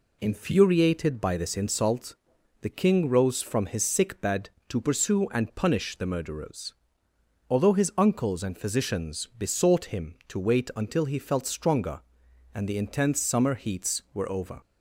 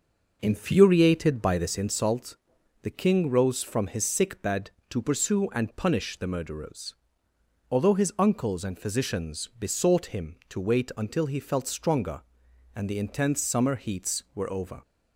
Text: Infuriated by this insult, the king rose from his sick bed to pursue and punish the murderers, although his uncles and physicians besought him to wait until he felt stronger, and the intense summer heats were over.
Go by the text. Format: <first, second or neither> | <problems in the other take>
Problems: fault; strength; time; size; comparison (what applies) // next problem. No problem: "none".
first | starts louder than the rest; noticeable; until 1.9 s; 5.5 dB